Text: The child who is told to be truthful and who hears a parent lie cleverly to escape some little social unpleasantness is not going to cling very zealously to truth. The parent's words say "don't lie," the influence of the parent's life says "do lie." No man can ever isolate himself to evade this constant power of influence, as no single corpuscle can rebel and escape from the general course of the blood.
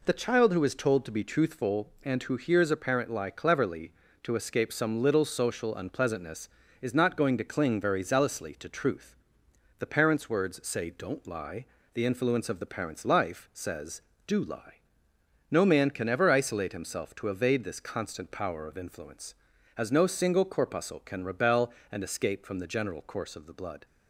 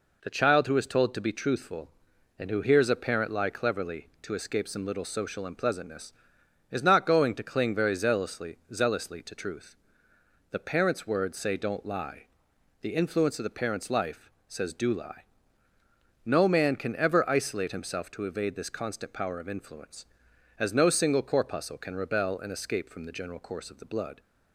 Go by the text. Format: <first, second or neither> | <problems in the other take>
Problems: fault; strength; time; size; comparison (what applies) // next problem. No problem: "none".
first | says "zealously" twice; at 8.7 s // pauses between "life" and "says"; slight; at 14.2 s; 0.20 s long